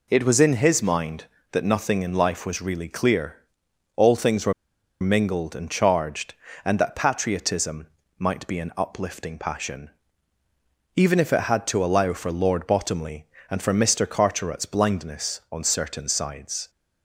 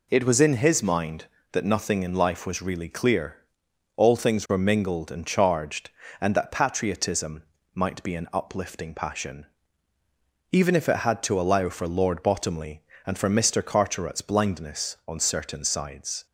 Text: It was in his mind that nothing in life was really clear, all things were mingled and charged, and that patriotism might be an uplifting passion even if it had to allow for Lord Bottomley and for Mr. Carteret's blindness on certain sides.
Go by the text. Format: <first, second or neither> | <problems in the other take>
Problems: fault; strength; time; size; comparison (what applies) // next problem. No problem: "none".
second | pauses between "were" and "mingled"; noticeable; at 4.5 s; 0.48 s long // pauses between "patriotism" and "might"; slight; at 7.8 s; 0.30 s long; slight in the second // pauses between "passion" and "even"; at 9.8 s; 1.0 s long; also in the second